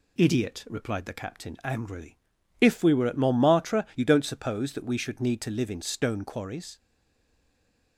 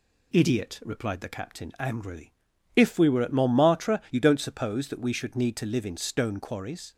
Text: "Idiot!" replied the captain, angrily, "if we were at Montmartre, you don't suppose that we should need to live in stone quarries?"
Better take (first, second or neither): second